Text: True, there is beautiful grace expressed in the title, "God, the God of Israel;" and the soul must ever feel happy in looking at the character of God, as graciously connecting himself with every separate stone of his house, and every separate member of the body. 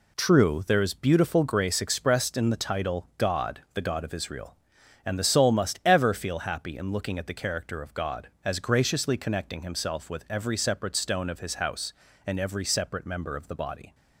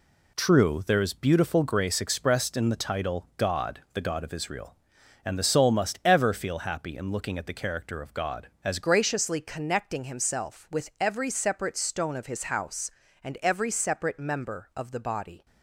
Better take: first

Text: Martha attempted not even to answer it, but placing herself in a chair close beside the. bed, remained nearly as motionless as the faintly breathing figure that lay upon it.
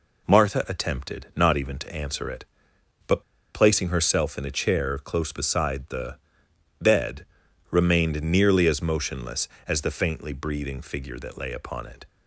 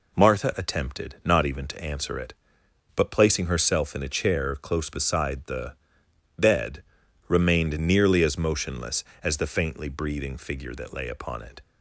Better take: second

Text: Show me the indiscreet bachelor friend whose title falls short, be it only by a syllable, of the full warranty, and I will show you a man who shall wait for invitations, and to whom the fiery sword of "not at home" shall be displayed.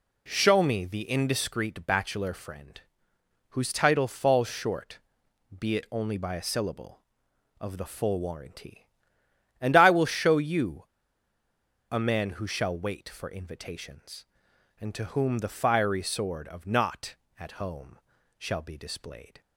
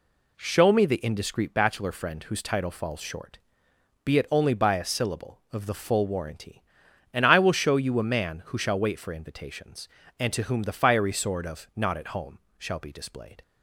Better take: second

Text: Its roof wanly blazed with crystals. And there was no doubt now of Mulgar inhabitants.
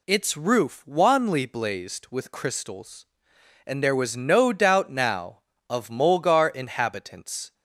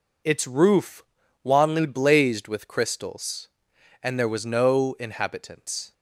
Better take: first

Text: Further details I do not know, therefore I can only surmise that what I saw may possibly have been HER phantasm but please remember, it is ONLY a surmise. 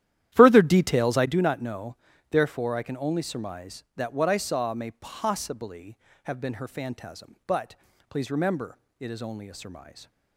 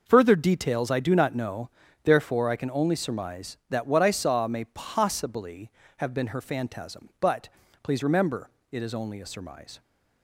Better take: second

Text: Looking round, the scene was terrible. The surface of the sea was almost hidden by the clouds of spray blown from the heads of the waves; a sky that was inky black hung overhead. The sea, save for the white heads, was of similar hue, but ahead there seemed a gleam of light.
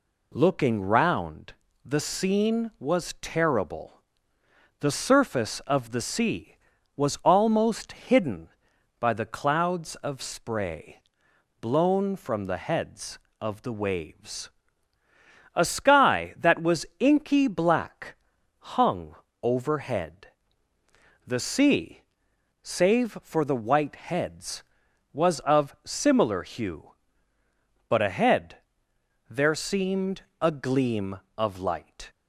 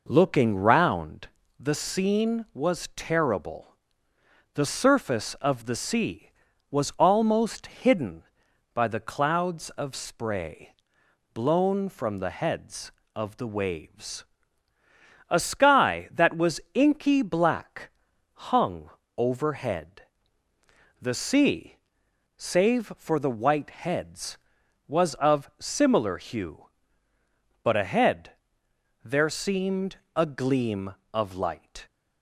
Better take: first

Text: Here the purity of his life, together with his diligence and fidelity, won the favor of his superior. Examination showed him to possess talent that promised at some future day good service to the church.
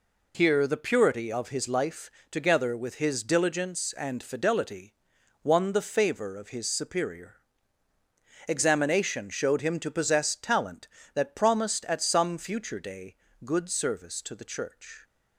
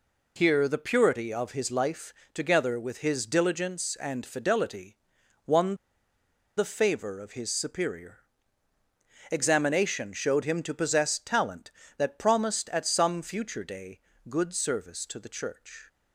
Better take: first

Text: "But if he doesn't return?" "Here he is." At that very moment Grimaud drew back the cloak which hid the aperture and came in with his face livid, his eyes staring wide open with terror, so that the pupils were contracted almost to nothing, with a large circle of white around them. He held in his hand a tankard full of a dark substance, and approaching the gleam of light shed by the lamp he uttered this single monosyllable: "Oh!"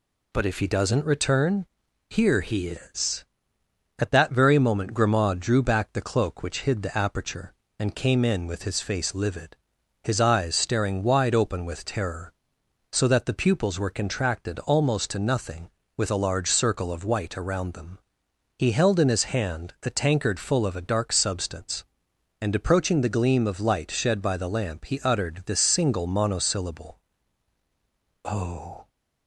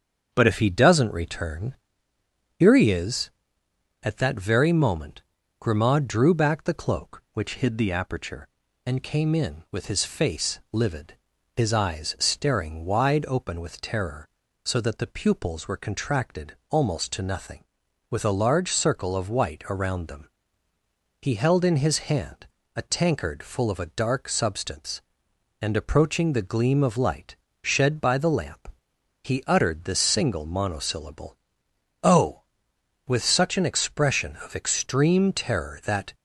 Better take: first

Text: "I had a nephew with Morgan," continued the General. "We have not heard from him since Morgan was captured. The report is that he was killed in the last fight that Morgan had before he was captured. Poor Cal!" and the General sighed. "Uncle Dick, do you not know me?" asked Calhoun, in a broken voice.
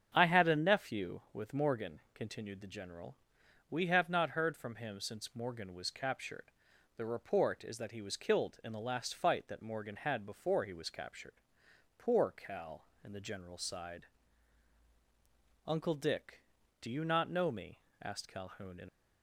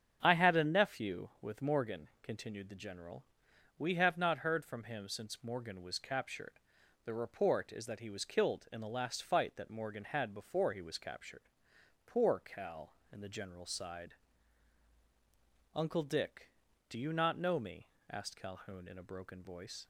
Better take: second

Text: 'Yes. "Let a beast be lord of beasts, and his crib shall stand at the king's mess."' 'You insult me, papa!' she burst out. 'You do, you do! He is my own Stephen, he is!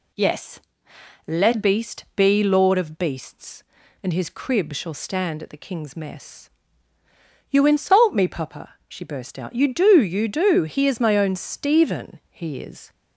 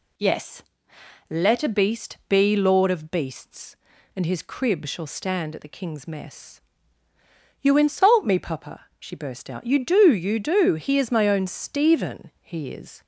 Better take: second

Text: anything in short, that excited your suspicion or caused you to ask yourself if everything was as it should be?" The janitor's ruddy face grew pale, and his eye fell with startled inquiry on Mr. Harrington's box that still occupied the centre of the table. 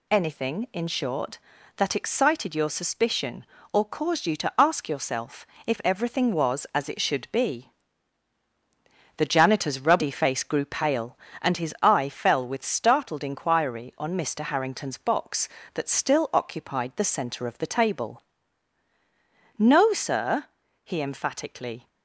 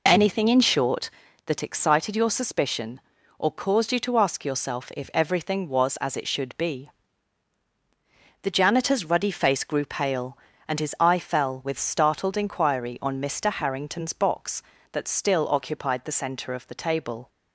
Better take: second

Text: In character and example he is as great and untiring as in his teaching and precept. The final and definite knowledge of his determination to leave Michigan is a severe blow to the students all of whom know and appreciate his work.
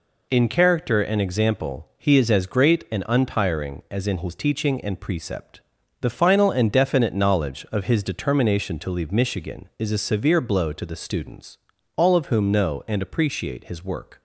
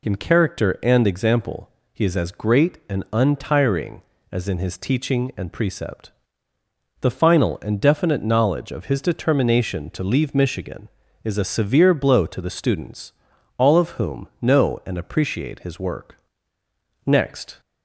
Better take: first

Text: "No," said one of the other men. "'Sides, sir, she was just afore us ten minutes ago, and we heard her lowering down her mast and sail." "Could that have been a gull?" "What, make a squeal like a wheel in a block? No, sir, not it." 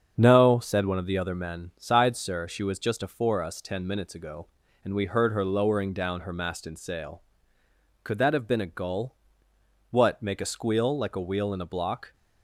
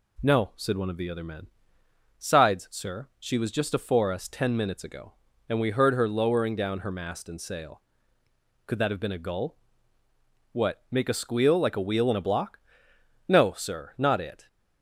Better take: second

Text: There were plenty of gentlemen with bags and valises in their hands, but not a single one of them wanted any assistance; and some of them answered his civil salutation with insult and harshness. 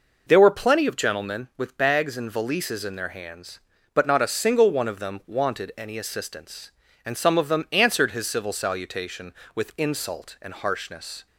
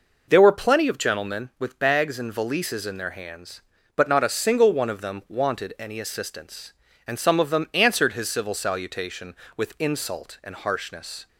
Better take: neither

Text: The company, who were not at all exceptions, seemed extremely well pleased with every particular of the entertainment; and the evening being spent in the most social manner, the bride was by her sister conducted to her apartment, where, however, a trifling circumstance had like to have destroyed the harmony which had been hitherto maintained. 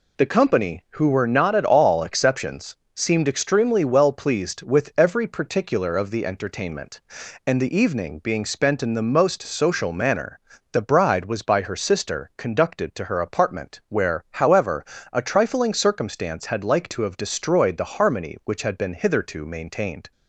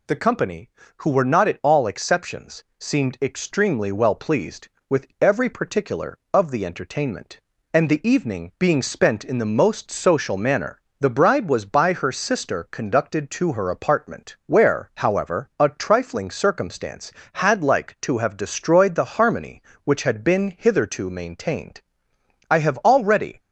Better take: first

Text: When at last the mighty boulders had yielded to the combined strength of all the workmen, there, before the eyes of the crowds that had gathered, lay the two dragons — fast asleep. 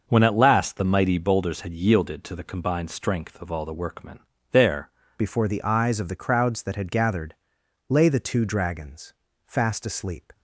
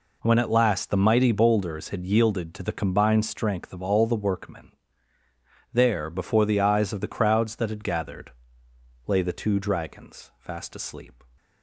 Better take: second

